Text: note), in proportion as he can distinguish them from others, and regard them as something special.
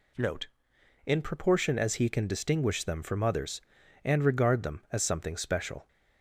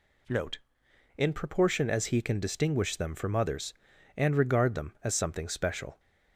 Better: neither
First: none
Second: none

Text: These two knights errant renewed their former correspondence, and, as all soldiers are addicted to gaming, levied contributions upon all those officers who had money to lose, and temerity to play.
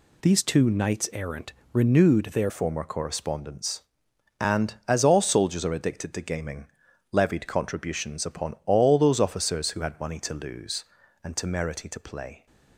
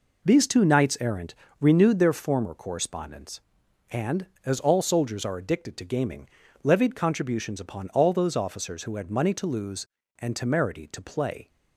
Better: second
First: pauses between "errant" and "renewed"; slight; at 1.5 s; 0.20 s long // changes voice at "former"; from 2.4 s on; 10.0 s long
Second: pauses between "errant" and "renewed"; slight; at 1.3 s; 0.26 s long

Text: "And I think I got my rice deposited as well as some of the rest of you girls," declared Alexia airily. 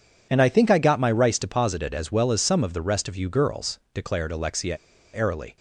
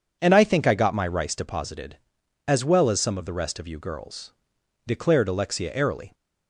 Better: second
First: pauses between "Alexia" and "airily"; at 4.7 s; 0.36 s long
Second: none

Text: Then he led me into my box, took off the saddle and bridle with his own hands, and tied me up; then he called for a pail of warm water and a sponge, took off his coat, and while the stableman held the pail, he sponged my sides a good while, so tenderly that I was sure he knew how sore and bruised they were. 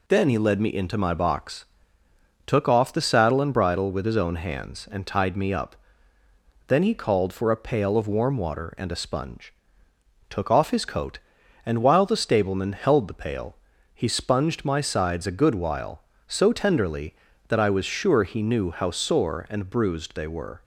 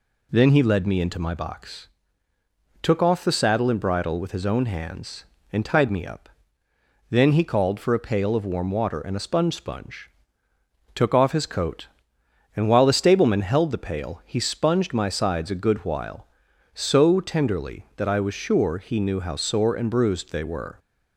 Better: first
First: none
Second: says "sponge" twice; at 9.5 s

